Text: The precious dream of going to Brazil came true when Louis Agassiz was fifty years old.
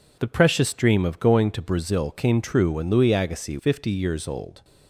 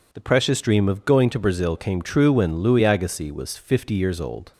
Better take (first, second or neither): second